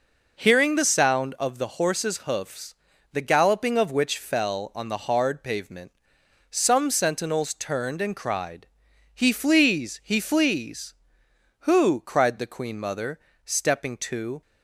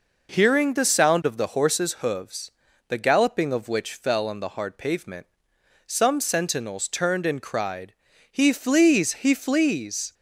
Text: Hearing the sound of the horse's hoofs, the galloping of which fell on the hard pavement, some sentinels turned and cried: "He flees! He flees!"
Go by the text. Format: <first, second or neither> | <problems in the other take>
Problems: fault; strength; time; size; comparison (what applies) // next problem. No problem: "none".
second | goes on to say "Who cried the queen mother stepping to"; strong; from 11.5 s on; 2.8 s long